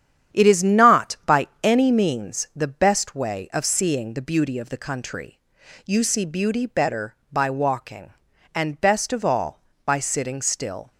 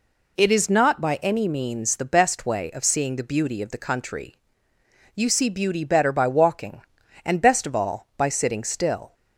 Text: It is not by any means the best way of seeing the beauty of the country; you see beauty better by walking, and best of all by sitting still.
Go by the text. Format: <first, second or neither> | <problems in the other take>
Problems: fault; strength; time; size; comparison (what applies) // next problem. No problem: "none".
second | gets quieter; throughout; 7 dB // pauses between "by" and "any"; slight; at 1.4 s; 0.16 s long